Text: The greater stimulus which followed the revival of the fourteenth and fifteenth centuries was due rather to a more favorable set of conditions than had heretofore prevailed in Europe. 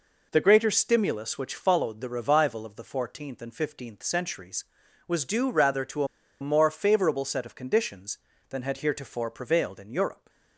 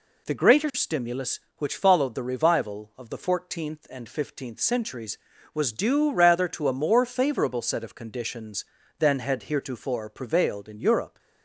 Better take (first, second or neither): second